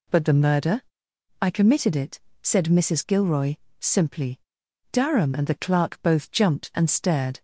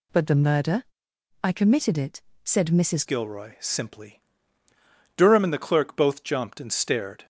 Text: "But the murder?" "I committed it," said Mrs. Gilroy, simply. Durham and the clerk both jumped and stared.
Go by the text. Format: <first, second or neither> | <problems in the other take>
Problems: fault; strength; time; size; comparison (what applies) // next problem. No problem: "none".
first | changes voice at "Gilroy"; from 3.0 s on; 4.2 s long